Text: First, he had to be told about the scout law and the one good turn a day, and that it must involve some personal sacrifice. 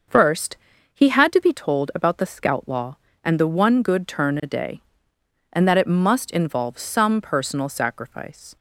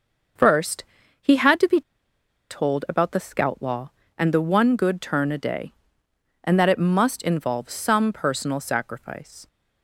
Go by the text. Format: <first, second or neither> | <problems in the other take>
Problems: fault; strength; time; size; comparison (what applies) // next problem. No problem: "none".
first | starts louder than the rest; until 1.7 s; 6.5 dB; also in the first // pauses between "be" and "told"; noticeable; at 1.8 s; 0.69 s long